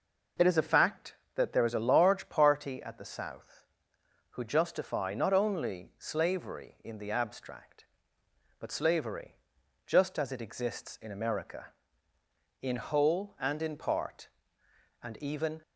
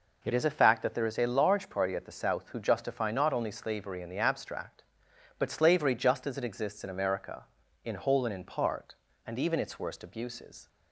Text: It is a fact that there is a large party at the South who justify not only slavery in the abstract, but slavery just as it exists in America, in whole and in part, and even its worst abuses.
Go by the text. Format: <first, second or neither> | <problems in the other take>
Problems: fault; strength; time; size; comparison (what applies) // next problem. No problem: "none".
second | pauses between "slavery" and "just"; noticeable; at 9.3 s; 0.50 s long // stops before "its worst abuses"; at 15.6 s